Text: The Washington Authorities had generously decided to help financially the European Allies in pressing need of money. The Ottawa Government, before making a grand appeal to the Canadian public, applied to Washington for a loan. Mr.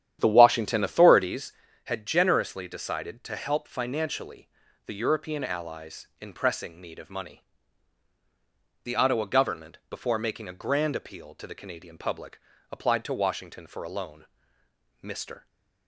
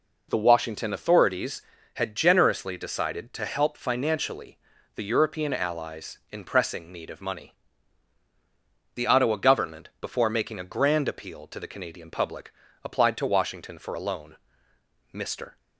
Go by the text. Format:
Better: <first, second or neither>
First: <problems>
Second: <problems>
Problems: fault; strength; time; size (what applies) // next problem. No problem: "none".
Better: second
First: starts louder than the rest; strong; until 1.4 s; 10 dB // pauses between "financially" and "the"; slight; at 4.4 s; 0.36 s long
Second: pauses between "financially" and "the"; slight; at 4.5 s; 0.36 s long